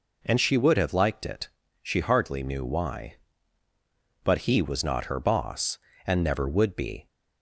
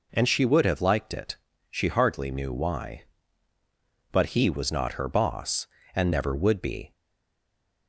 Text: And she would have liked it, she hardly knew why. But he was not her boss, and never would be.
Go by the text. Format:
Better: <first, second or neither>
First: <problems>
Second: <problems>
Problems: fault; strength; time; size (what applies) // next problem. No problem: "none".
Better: first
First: none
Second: stays silent after the last word; from 6.9 s on; 0.9 s long